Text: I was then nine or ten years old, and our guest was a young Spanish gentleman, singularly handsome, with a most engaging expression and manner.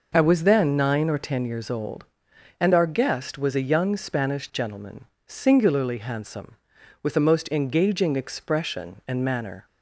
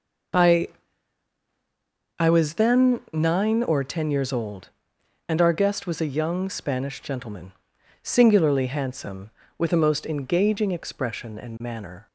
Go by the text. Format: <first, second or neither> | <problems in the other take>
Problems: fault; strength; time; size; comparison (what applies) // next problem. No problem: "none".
first | says "I" twice; at 2.1 s